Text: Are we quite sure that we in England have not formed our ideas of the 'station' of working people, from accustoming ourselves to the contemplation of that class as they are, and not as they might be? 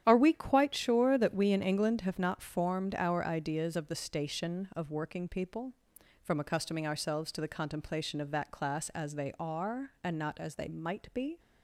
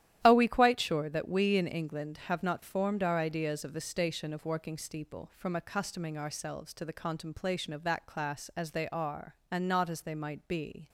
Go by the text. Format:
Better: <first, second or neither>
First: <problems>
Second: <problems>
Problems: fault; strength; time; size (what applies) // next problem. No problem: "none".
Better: first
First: starts louder than the rest; strong; until 1.0 s; 10 dB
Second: starts louder than the rest; strong; until 1.2 s; 11.5 dB // says "steeple" for "people"; at 4.7 s